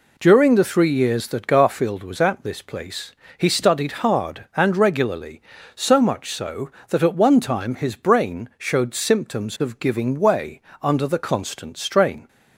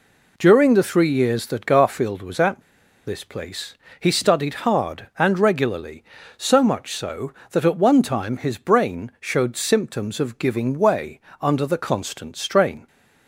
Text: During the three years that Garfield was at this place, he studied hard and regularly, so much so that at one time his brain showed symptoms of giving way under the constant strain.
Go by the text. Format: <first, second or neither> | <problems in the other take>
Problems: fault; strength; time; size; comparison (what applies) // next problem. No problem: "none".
first | pauses between "at" and "this"; at 2.6 s; 0.44 s long // pauses between "way" and "under"; slight; at 11.1 s; 0.22 s long; slight in the first